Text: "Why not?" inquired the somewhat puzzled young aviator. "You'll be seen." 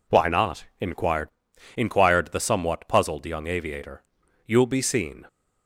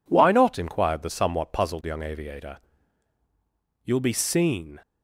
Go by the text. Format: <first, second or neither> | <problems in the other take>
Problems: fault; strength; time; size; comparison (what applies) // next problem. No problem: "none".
second | says "inquired" twice; at 1.7 s